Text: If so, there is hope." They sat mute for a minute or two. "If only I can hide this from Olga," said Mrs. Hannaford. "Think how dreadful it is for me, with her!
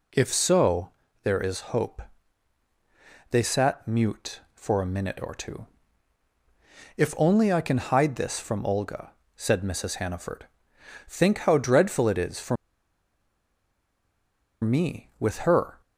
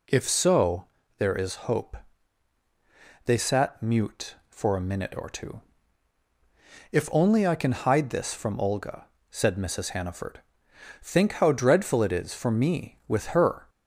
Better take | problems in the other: second | pauses between "for" and "me"; strong; at 12.5 s; 2.0 s long

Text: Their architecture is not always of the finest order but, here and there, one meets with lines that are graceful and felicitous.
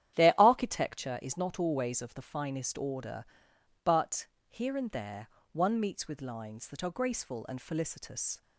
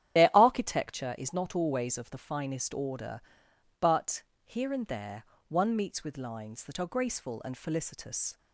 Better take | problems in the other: first | loses the start of "Their"; at 0.1 s; 45 ms // starts louder than the rest; strong; until 1.2 s; 10.5 dB; strong in the first

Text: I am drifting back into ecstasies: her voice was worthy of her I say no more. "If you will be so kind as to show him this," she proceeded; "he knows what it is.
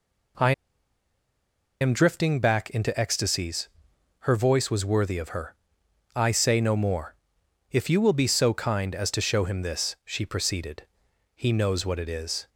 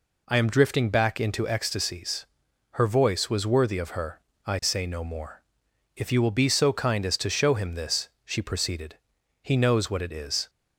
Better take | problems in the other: second | pauses between "I" and "am"; strong; at 0.5 s; 1.2 s long // pauses between "her" and "I"; noticeable; at 5.5 s; 0.58 s long; slight in the second

